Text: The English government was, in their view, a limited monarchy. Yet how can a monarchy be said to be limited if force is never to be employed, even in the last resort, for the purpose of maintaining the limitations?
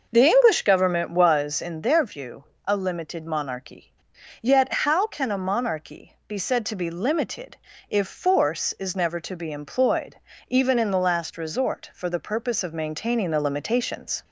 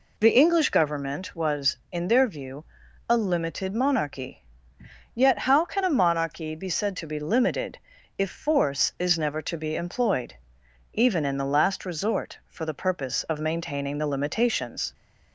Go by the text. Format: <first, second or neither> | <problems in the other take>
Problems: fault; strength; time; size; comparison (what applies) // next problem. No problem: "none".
second | starts louder than the rest; noticeable; until 1.9 s; 6 dB // pauses between "limited" and "if"; slight; at 7.5 s; 0.32 s long; also in the second